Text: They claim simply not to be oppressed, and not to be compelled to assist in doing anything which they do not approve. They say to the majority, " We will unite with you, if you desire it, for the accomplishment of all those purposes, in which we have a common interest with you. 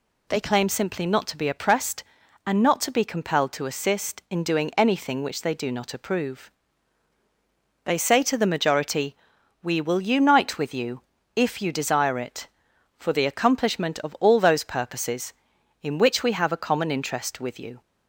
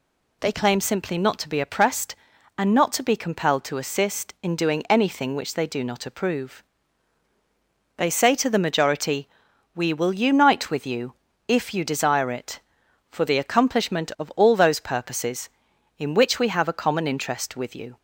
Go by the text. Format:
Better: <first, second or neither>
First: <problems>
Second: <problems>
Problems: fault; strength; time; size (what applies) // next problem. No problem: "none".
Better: neither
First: none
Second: none